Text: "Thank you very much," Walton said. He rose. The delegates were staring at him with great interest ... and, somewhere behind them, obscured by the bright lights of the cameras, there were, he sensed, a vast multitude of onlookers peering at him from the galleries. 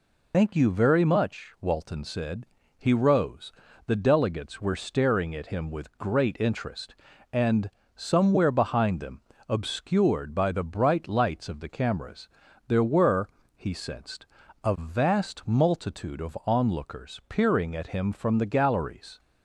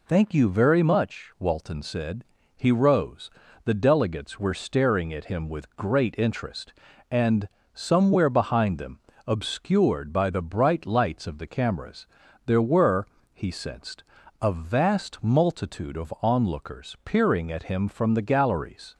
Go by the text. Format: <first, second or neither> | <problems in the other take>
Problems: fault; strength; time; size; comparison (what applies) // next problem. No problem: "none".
second | loses the start of "Thank"; at 0.3 s; 50 ms